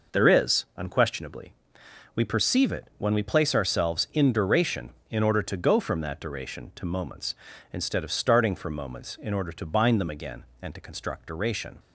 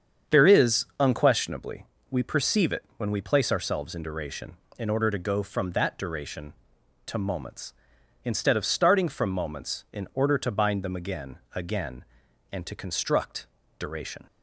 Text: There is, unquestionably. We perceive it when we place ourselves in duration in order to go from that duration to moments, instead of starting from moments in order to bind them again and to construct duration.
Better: first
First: none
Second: starts louder than the rest; strong; until 1.4 s; 7.5 dB // says "again" twice; at 11.5 s // pauses between "construct" and "duration"; slight; at 13.4 s; 0.32 s long

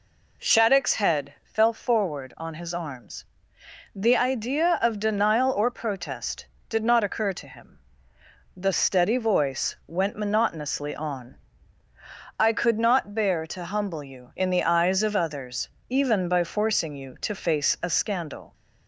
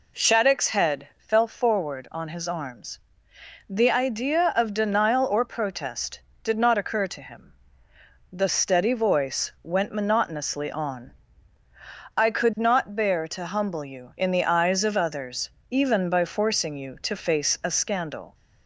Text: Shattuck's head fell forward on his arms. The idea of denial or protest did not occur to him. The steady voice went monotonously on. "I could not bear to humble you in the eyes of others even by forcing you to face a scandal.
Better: neither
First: pauses between "others" and "even"; slight; at 15.6 s; 0.20 s long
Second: pauses between "others" and "even"; slight; at 15.4 s; 0.20 s long

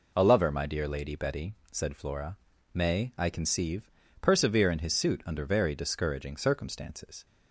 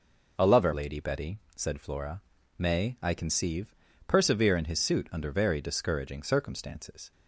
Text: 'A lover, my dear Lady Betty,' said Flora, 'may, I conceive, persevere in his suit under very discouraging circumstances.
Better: first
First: none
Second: skips "my dear"; at 0.7 s

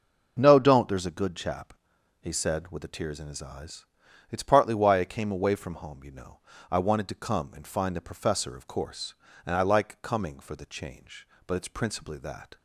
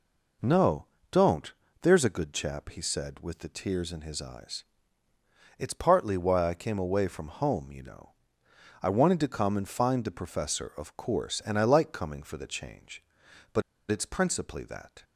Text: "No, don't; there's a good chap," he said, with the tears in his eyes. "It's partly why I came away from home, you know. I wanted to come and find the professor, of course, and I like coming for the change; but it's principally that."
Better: first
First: none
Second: pauses between "but" and "it's"; slight; at 13.6 s; 0.29 s long

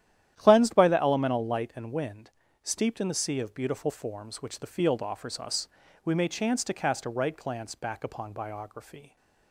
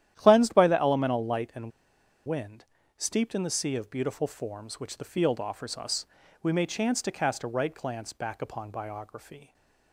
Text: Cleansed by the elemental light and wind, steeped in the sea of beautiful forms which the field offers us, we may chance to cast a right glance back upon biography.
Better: first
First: starts louder than the rest; strong; until 1.3 s; 11.5 dB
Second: starts louder than the rest; strong; until 1.1 s; 11.5 dB // pauses between "and" and "wind"; noticeable; at 1.7 s; 0.56 s long

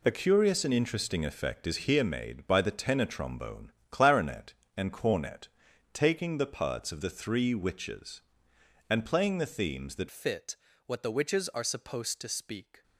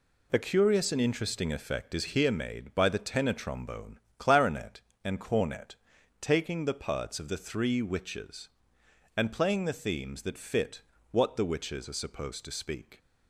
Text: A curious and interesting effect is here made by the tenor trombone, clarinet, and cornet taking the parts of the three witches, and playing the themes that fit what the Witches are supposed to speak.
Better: second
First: pauses between "cornet" and "taking"; noticeable; at 5.4 s; 0.46 s long // changes voice at "fit"; from 10.1 s on; 2.7 s long // pauses between "fit" and "what"; slight; at 10.5 s; 0.30 s long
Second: pauses between "cornet" and "taking"; noticeable; at 5.7 s; 0.46 s long // pauses between "fit" and "what"; slight; at 10.8 s; 0.28 s long

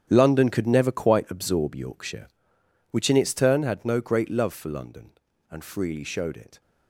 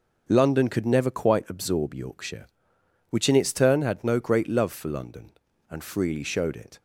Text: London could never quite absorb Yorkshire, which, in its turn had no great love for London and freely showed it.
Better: second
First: gets quieter; strong; throughout; 12.5 dB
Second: none

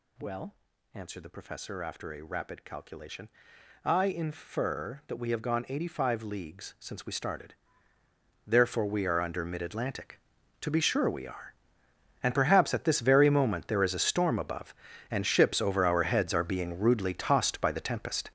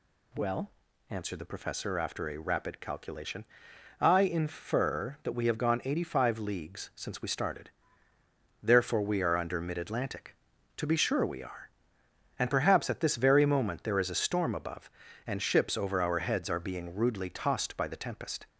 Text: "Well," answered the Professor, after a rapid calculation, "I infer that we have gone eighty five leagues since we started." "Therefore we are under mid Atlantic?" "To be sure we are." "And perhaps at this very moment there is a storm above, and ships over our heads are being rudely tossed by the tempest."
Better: second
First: gets louder; strong; throughout; 11 dB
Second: none

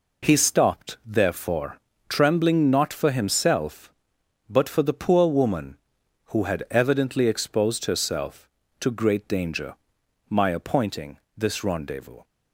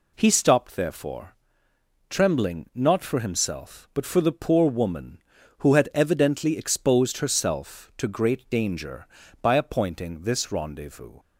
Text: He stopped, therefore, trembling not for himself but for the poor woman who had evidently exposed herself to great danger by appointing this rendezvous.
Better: second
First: says "my" for "by"; at 10.2 s // pauses between "appointing" and "this"; slight; at 11.1 s; 0.18 s long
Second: none

